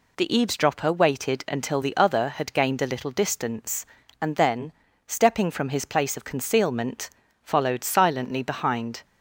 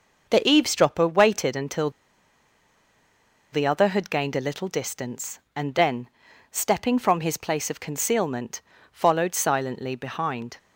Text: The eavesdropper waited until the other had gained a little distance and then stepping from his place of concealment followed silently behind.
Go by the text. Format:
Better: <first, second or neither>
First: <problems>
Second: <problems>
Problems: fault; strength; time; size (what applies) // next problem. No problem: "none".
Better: first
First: pauses between "then" and "stepping"; slight; at 4.7 s; 0.36 s long // pauses between "concealment" and "followed"; slight; at 7.0 s; 0.34 s long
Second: starts louder than the rest; noticeable; until 1.3 s; 6 dB // pauses between "until" and "the"; strong; at 1.8 s; 1.6 s long // pauses between "then" and "stepping"; at 6.0 s; 0.42 s long // pauses between "concealment" and "followed"; slight; at 8.5 s; 0.32 s long